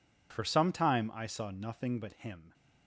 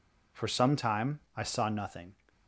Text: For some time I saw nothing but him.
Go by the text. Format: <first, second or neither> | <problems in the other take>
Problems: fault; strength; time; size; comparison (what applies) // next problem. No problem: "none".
first | pauses between "time" and "I"; slight; at 1.1 s; 0.16 s long // stops before "but him"; at 2.2 s